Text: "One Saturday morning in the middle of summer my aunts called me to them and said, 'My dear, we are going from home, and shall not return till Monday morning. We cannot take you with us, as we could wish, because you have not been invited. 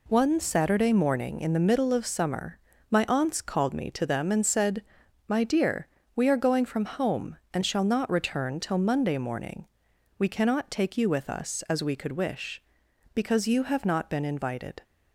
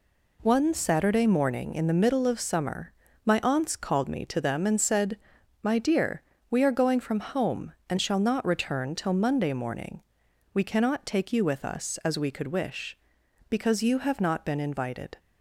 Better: neither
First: pauses between "summer" and "my"; slight; at 2.5 s; 0.33 s long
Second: pauses between "summer" and "my"; slight; at 2.9 s; 0.34 s long

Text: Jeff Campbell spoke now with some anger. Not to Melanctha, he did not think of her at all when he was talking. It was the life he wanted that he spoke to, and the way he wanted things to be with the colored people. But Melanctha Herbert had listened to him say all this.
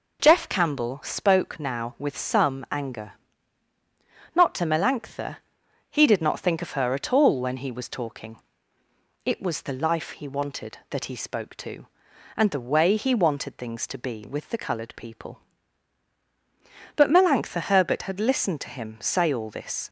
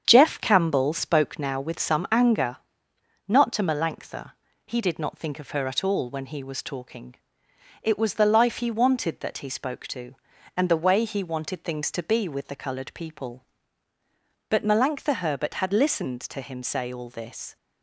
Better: first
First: none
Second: starts louder than the rest; strong; until 1.7 s; 8 dB

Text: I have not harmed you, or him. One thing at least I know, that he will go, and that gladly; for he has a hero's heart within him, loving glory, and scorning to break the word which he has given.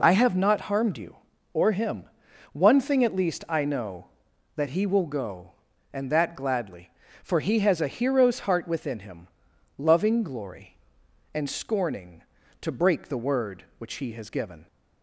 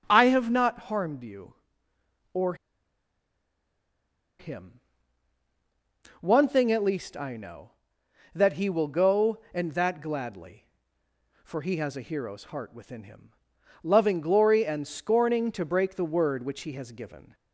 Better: first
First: none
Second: starts louder than the rest; strong; until 1.0 s; 7 dB // pauses between "or" and "him"; strong; at 2.5 s; 1.8 s long

